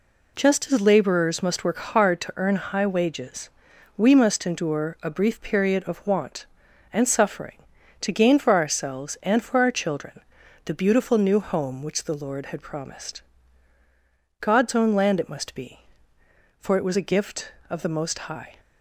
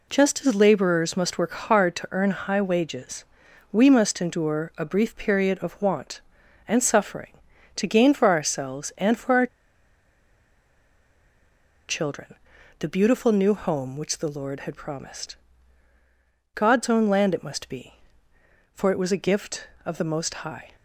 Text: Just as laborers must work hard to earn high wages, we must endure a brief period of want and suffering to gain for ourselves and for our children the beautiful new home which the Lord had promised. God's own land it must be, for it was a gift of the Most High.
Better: first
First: pauses between "children" and "the"; at 10.2 s; 0.44 s long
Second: pauses between "our" and "children"; strong; at 9.4 s; 2.4 s long // pauses between "children" and "the"; at 12.3 s; 0.44 s long

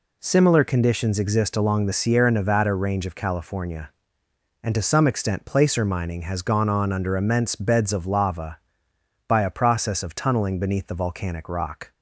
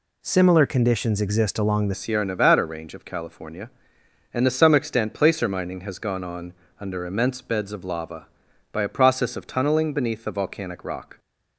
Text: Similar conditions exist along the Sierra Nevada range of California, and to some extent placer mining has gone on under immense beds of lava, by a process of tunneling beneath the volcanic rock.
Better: first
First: none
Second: changes voice at "Sierra"; from 1.9 s on; 9.2 s long // pauses between "on" and "under"; slight; at 6.5 s; 0.26 s long

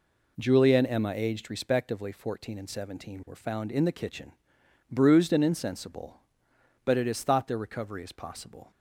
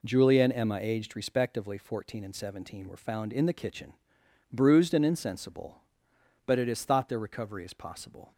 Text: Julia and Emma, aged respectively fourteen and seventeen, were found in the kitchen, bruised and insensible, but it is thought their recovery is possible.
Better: neither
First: none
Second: none

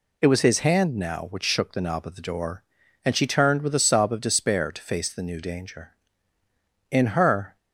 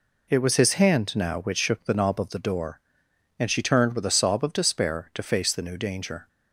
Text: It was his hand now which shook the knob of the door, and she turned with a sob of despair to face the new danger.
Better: second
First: goes on to say "In her"; noticeable; from 6.9 s on; 0.66 s long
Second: none

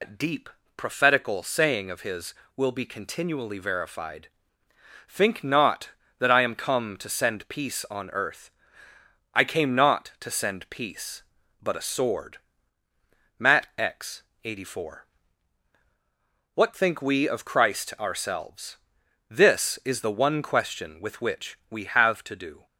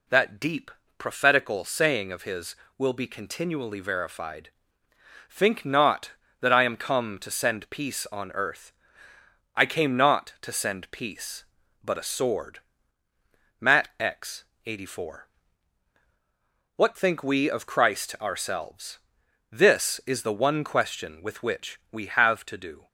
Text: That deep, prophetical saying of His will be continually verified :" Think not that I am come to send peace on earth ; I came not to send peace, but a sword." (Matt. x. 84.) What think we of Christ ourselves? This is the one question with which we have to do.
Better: second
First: loses the start of "That"; at 0.0 s; 140 ms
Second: none

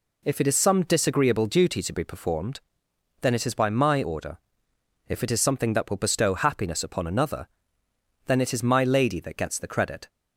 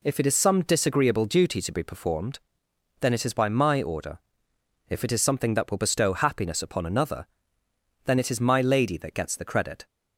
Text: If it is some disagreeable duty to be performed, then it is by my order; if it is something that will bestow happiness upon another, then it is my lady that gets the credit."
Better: neither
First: none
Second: none

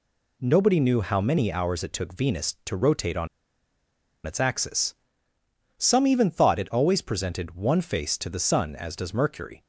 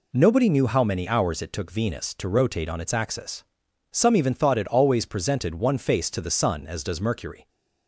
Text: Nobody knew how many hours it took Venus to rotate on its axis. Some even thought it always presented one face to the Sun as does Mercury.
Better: second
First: pauses between "on" and "its"; at 3.2 s; 0.99 s long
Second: none

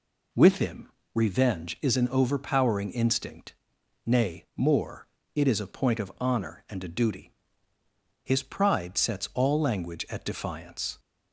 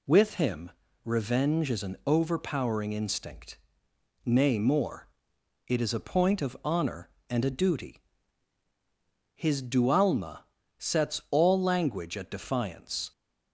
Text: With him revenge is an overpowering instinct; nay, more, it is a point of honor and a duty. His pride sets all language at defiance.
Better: first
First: pauses between "him" and "revenge"; slight; at 0.8 s; 0.24 s long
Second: pauses between "him" and "revenge"; slight; at 0.7 s; 0.32 s long // says "dualma" for "pride"; at 9.6 s

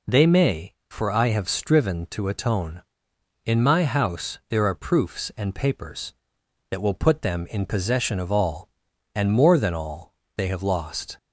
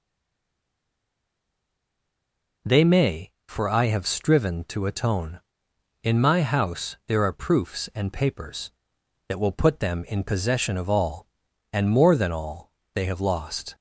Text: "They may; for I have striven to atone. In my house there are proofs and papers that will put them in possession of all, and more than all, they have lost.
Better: first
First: none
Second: stays silent before the first word; strong; until 2.6 s; 2.6 s long

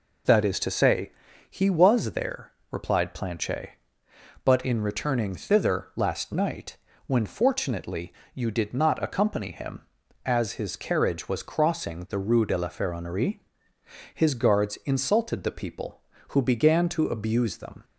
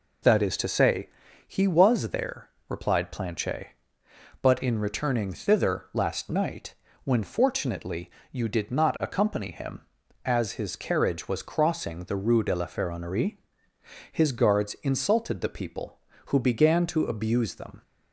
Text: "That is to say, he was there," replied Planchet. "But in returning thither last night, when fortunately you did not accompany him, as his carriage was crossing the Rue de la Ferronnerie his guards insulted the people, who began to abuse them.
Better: neither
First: pauses between "fortunately" and "you"; slight; at 8.1 s; 0.22 s long // pauses between "Ferronnerie" and "his"; noticeable; at 13.4 s; 0.74 s long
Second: pauses between "fortunately" and "you"; slight; at 8.0 s; 0.22 s long // pauses between "Ferronnerie" and "his"; noticeable; at 13.3 s; 0.74 s long

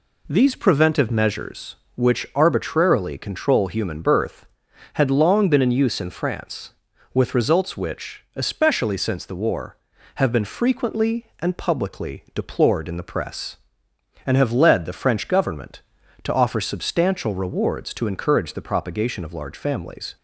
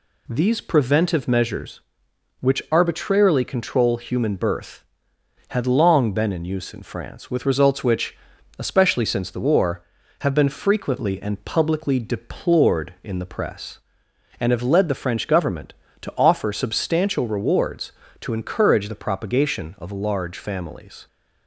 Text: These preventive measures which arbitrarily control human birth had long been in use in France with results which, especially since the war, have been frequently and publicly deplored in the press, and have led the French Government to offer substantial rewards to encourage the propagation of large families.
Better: neither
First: none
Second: none

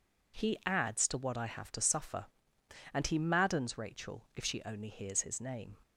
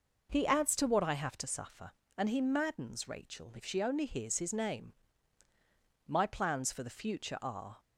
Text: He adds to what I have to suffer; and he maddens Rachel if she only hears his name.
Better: first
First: none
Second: goes on to say "My plans for the future are"; strong; from 6.0 s on; 1.7 s long

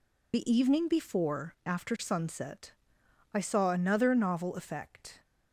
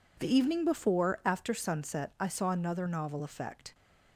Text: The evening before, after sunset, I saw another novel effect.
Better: second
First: loses the start of "The"; at 0.3 s; 75 ms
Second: none

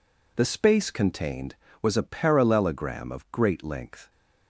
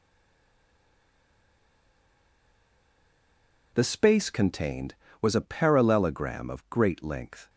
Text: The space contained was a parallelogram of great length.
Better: first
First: none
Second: stays silent before the first word; strong; until 3.7 s; 3.7 s long

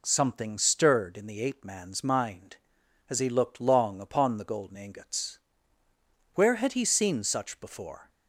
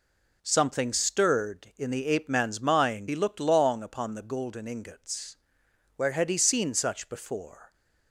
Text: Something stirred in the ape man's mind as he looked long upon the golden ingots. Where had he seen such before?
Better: first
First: none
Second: skips "as"; at 3.0 s

